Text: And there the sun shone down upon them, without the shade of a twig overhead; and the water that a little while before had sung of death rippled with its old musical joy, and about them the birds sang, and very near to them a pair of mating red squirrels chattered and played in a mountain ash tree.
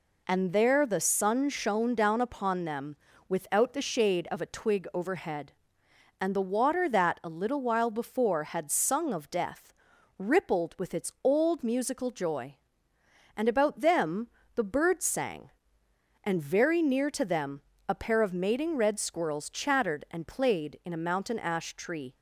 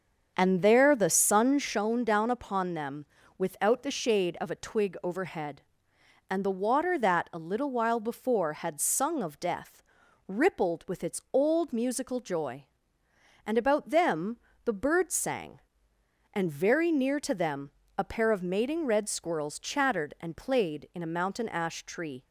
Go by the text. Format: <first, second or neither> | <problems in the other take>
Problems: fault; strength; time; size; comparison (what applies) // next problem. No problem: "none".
first | starts louder than the rest; until 1.7 s; 6.5 dB // pauses between "death" and "rippled"; noticeable; at 9.8 s; 0.46 s long; noticeable in the first // pauses between "them" and "the"; slight; at 14.3 s; 0.26 s long; slight in the first // pauses between "them" and "a"; slight; at 17.6 s; 0.28 s long; slight in the first